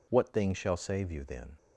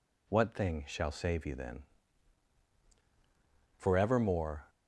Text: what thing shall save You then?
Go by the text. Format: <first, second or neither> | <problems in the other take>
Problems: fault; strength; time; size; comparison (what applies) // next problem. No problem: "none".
first | goes on to say "forevermore"; noticeable; from 3.7 s on; 0.94 s long